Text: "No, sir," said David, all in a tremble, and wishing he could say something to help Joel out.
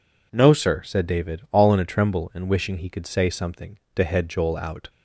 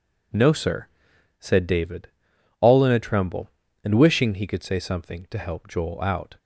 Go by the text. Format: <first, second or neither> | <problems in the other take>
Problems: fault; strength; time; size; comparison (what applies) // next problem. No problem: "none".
second | says "head" for "help"; at 4.0 s